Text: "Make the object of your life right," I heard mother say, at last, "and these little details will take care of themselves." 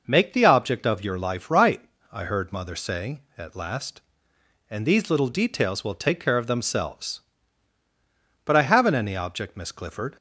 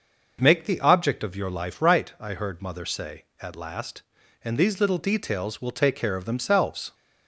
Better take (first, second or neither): second